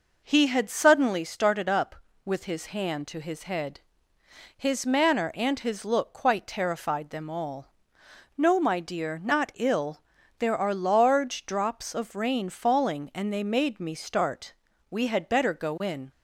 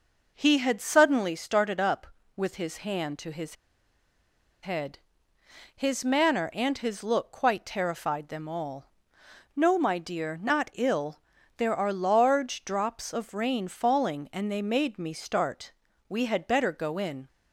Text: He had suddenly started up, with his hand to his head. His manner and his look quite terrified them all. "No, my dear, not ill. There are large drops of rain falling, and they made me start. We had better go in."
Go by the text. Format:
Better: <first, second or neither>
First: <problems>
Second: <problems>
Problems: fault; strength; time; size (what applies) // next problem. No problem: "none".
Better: first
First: none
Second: pauses between "his" and "head"; at 3.5 s; 1.0 s long